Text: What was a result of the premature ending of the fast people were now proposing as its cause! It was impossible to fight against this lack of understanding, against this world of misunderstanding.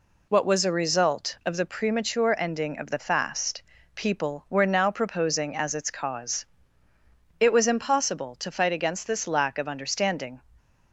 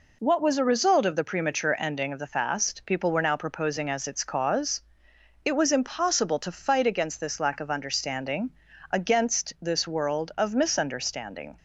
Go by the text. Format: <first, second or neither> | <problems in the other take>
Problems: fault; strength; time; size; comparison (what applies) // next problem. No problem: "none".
second | pauses between "fast" and "people"; slight; at 3.6 s; 0.32 s long // stops before "against this world of misunderstanding"; at 10.5 s